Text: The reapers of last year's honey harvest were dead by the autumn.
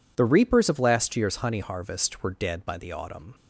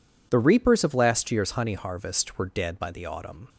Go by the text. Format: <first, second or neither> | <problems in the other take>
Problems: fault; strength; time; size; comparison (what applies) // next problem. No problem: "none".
neither | none